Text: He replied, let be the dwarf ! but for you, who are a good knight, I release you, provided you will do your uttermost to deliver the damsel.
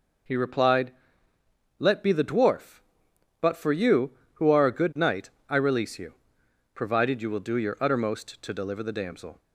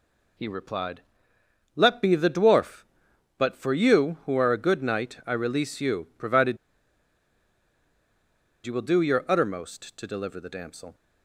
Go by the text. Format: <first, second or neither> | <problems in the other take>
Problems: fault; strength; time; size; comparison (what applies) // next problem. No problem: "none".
first | pauses between "provided" and "you"; strong; at 6.5 s; 2.0 s long